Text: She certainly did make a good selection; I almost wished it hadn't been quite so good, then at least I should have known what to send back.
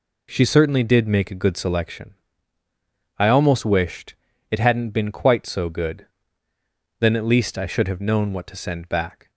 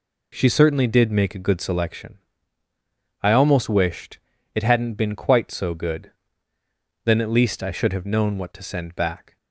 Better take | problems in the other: neither | pauses between "wished" and "it"; the same in both

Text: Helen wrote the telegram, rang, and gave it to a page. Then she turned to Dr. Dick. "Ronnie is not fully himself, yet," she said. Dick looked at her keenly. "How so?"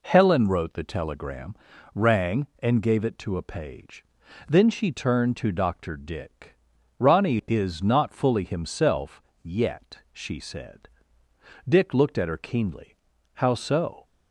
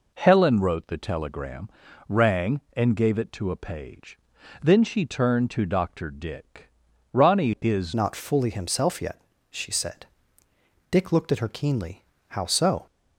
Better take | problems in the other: first | changes voice at "not"; from 7.9 s on; 4.9 s long

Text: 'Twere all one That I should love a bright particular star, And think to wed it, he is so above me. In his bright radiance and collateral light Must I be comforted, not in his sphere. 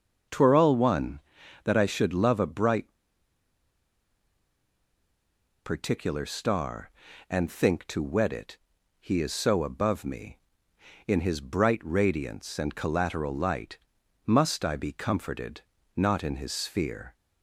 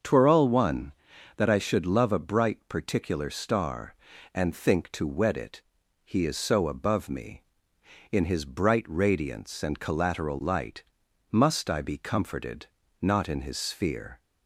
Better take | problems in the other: second | starts louder than the rest; until 1.7 s; 6 dB; also in the second // pauses between "bright" and "particular"; strong; at 2.9 s; 2.7 s long // pauses between "light" and "Must"; noticeable; at 13.7 s; 0.48 s long; noticeable in the second

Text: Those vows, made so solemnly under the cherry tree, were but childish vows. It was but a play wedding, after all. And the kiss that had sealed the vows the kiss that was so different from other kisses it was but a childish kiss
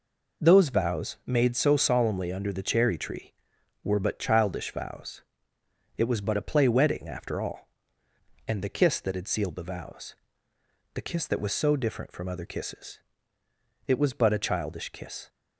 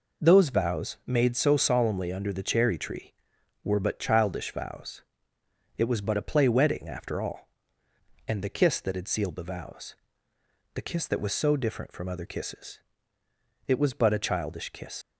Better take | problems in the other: first | pauses between "vows" and "the"; noticeable; at 9.9 s; 0.80 s long; noticeable in the first // pauses between "kisses" and "it"; noticeable; at 12.7 s; 0.88 s long; noticeable in the first // leaves "kiss" unfinished; at 15.0 s; 70 ms

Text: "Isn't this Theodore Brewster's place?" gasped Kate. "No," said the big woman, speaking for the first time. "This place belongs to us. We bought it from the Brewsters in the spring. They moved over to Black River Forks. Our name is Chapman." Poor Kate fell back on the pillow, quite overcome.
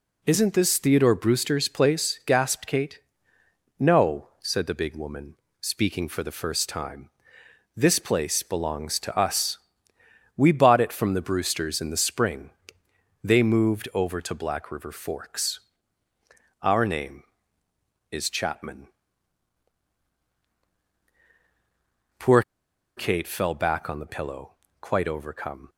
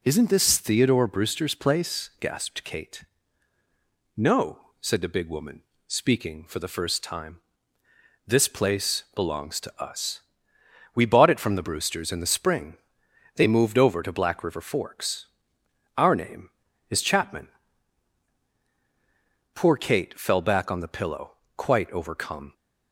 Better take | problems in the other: second | pauses between "Poor" and "Kate"; noticeable; at 22.4 s; 0.54 s long

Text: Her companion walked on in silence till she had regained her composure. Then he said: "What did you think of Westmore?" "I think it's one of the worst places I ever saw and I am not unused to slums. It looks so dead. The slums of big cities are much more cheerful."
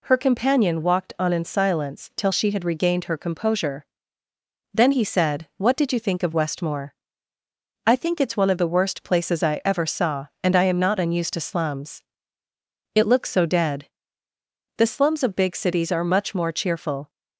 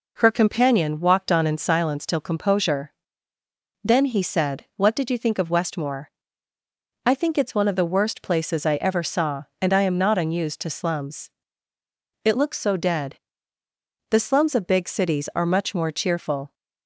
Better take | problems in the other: first | skips "she had regained her"; at 2.2 s

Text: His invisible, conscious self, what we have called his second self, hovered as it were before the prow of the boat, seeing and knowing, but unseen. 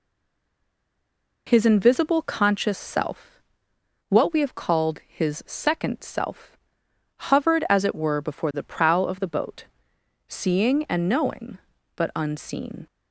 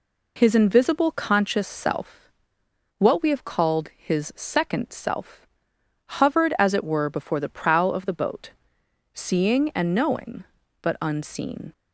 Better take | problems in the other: second | stays silent before the first word; noticeable; until 1.4 s; 1.4 s long

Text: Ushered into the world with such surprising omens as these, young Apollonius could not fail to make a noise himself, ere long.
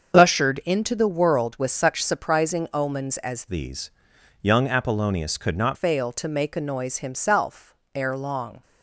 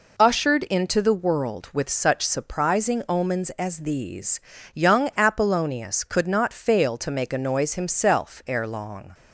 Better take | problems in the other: second | starts louder than the rest; until 1.2 s; 7 dB // changes voice from "these" to "not"; from 3.4 to 5.7 s; 2.3 s long

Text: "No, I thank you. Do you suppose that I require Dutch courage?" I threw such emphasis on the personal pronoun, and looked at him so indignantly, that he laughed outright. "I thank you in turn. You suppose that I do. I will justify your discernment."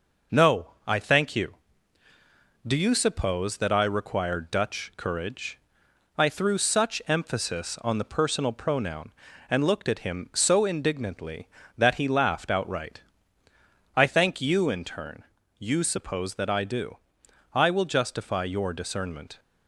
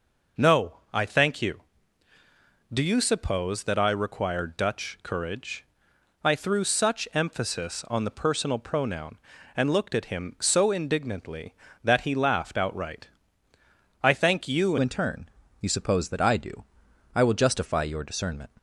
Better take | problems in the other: first | changes voice at "in"; from 14.8 s on; 3.6 s long

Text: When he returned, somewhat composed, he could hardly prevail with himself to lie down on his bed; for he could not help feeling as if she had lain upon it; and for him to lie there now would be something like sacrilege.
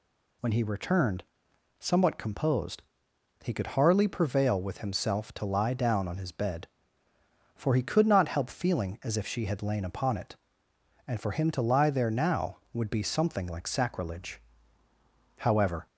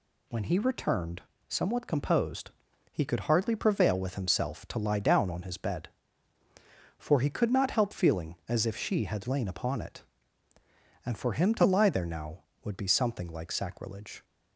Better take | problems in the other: second | goes on to say "However"; slight; from 15.3 s on; 0.46 s long

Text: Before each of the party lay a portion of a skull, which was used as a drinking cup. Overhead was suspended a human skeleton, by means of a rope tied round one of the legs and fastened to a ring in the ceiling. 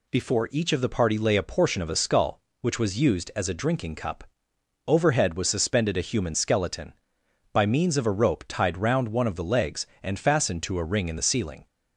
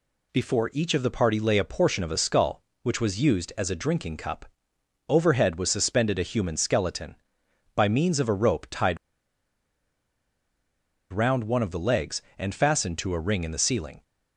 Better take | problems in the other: first | pauses between "tied" and "round"; strong; at 8.9 s; 2.1 s long

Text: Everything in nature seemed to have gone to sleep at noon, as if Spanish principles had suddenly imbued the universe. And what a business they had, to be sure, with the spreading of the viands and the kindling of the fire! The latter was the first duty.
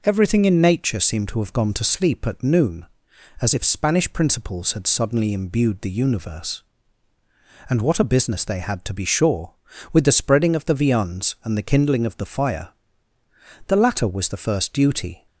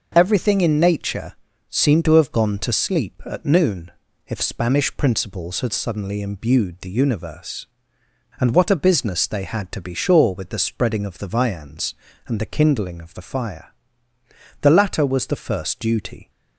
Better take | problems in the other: first | pauses between "nature" and "seemed"; slight; at 1.3 s; 0.36 s long // skips "as"; at 4.0 s

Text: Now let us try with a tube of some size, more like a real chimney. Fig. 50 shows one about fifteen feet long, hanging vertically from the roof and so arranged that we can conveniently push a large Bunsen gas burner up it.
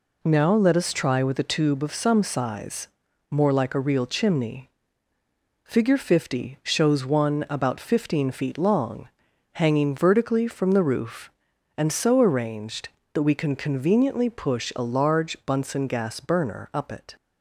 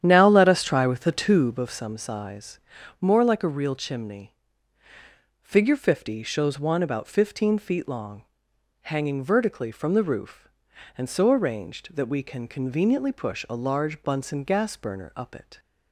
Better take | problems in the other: first | starts louder than the rest; strong; until 1.8 s; 9.5 dB

